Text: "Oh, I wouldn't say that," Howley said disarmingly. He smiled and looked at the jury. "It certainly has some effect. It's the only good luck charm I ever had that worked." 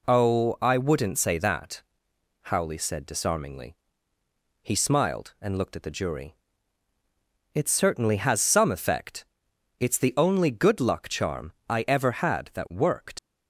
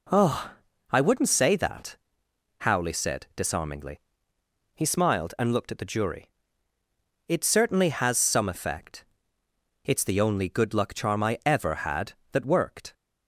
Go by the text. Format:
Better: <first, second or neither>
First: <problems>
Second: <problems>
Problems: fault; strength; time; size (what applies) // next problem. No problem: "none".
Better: second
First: pauses between "charm" and "I"; slight; at 11.5 s; 0.18 s long // leaves "worked" unfinished; at 13.1 s; 80 ms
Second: none